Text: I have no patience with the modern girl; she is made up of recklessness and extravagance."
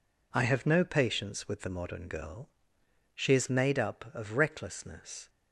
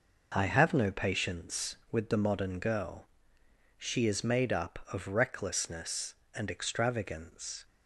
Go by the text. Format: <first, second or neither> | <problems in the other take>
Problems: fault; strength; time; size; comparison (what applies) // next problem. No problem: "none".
second | stops before "and extravagance"; at 5.2 s